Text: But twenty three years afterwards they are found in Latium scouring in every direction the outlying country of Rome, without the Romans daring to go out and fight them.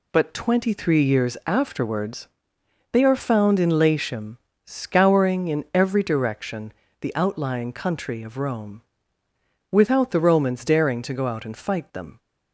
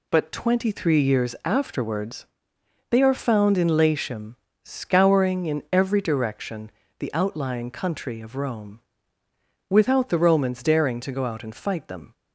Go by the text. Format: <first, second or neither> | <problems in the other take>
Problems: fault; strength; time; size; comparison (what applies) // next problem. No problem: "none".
neither | pauses between "afterwards" and "they"; noticeable; the same in both // pauses between "Latium" and "scouring"; slight; the same in both // pauses between "direction" and "the"; slight; the same in both